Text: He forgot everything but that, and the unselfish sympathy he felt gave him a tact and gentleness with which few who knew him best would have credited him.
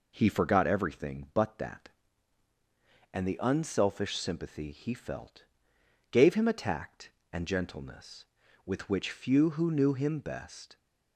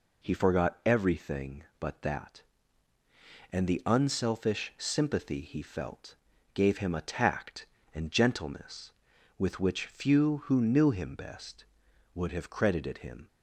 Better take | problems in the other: second | pauses between "felt" and "gave"; noticeable; at 5.4 s; 0.66 s long; also in the second // stops before "would have credited him"; at 10.7 s

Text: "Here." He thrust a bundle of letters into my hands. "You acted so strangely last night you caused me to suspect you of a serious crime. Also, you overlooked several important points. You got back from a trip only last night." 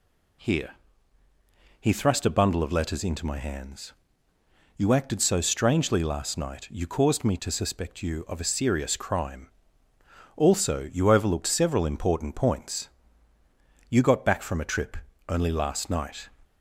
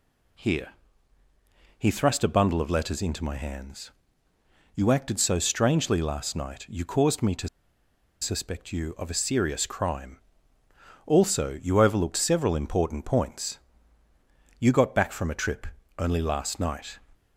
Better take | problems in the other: first | pauses between "to" and "suspect"; noticeable; at 7.4 s; 0.73 s long // pauses between "trip" and "only"; slight; at 15.6 s; 0.32 s long; slight in the first

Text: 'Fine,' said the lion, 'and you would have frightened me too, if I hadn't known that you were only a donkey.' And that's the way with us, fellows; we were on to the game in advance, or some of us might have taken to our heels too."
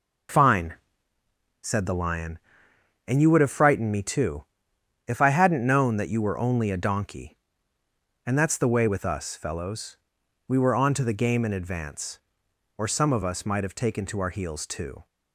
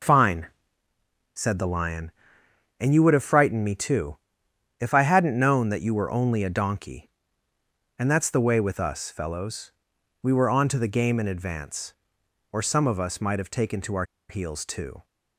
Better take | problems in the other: first | pauses between "our" and "heels"; slight; at 14.0 s; 0.26 s long

